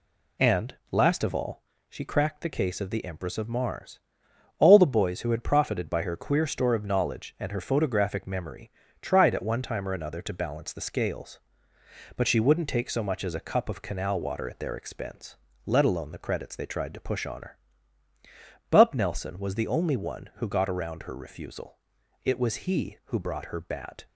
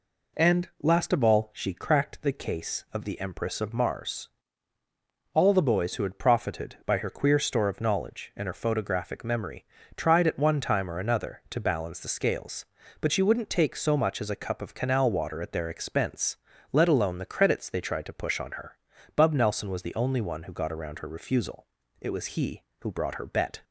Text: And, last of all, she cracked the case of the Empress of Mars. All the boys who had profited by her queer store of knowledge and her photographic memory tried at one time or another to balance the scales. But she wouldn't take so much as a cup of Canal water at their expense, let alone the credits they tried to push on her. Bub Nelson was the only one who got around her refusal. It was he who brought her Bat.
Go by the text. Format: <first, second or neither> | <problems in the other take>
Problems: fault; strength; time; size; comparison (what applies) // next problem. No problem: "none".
first | pauses between "memory" and "tried"; slight; at 9.6 s; 0.32 s long; slight in the first // says "Bet" for "Bat"; at 23.2 s